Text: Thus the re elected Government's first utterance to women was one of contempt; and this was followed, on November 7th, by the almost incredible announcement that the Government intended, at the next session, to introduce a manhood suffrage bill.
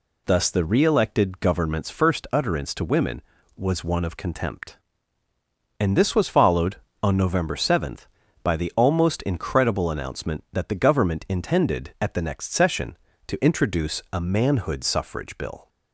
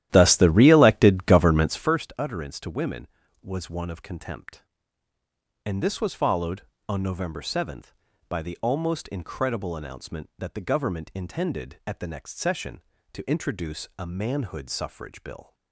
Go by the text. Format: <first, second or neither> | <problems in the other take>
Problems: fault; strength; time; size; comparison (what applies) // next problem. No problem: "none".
first | starts louder than the rest; strong; until 2.0 s; 13 dB